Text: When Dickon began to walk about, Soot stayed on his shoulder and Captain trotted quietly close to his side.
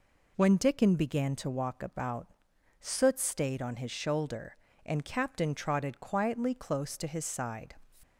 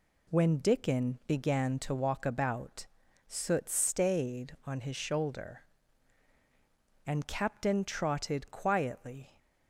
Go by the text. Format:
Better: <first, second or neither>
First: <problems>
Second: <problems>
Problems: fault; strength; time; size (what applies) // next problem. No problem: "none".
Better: first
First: none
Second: stops before "close to his side"; at 9.3 s